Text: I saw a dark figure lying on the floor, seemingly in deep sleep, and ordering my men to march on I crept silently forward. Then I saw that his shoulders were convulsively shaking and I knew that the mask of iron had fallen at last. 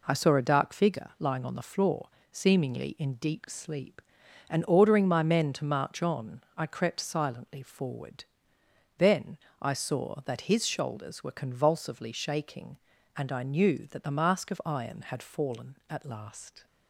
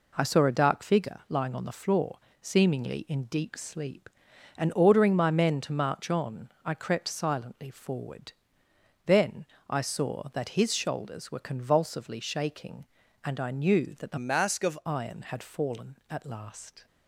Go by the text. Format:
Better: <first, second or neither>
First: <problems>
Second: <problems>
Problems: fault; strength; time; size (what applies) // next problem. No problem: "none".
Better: first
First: pauses between "Then" and "I"; slight; at 9.3 s; 0.22 s long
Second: pauses between "Then" and "I"; slight; at 9.4 s; 0.22 s long // changes voice from "mask" to "of"; from 14.1 to 14.7 s; 0.6 s long